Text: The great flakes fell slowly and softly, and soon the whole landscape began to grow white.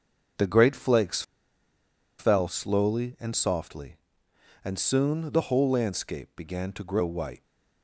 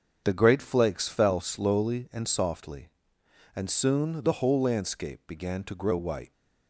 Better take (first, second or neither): second